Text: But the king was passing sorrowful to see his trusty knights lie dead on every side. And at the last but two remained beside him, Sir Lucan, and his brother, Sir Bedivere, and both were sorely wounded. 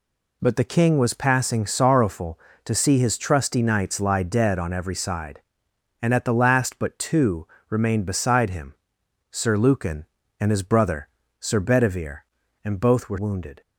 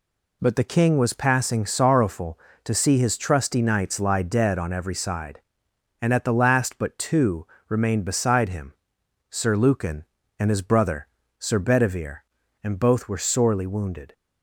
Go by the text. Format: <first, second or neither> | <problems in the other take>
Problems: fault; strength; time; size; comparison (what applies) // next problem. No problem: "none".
second | pauses between "two" and "remained"; slight; at 7.4 s; 0.22 s long; slight in the second // skips "sorely"; at 13.1 s